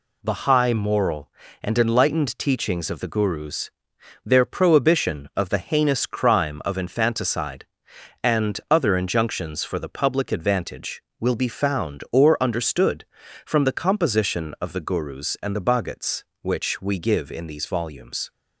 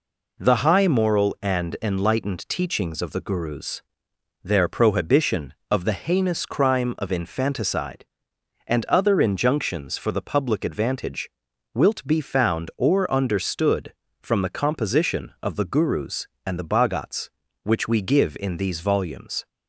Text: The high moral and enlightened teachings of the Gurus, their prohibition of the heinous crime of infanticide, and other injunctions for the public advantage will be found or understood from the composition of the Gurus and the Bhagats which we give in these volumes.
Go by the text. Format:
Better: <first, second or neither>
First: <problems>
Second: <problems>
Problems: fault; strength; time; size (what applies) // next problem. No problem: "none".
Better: first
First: none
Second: says "wilt" for "will"; at 11.7 s